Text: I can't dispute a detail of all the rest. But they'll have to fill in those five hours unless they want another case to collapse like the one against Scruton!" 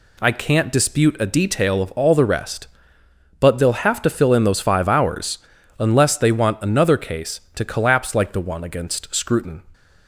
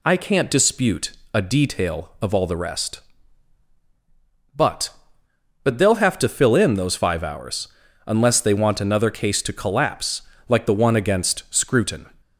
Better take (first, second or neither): first